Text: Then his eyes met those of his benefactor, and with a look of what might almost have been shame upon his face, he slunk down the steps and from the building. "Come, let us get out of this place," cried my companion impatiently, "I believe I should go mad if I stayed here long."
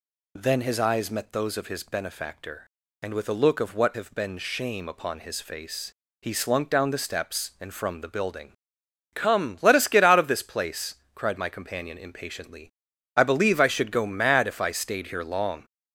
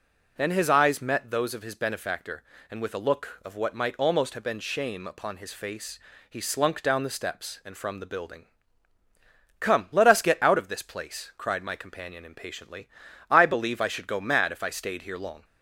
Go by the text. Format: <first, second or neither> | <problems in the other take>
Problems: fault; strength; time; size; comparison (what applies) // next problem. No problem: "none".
second | skips "might almost"; at 3.9 s